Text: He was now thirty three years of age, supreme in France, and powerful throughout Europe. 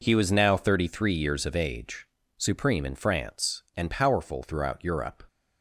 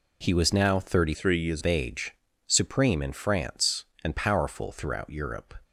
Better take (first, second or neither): first